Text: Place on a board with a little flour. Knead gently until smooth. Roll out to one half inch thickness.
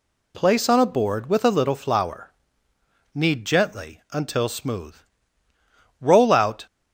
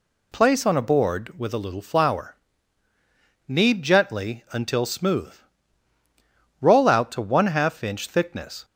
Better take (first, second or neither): second